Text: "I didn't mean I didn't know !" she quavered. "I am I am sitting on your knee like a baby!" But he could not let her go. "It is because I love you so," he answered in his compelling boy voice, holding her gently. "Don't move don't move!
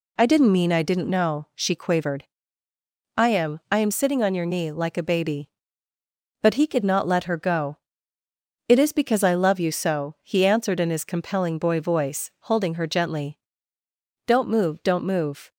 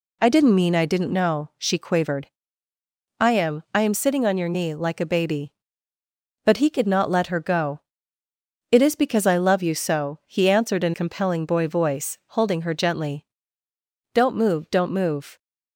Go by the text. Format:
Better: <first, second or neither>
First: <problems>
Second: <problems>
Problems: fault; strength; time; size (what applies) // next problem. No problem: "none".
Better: first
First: none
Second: skips "his"; at 10.9 s